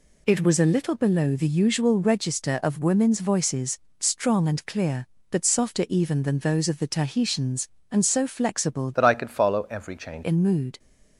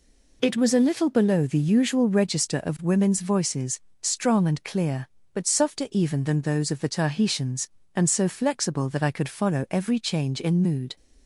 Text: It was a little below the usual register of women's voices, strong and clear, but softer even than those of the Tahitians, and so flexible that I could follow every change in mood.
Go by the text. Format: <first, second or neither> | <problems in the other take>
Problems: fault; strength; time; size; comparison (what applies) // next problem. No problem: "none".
second | changes voice from "that" to "change"; from 8.9 to 10.2 s; 1.3 s long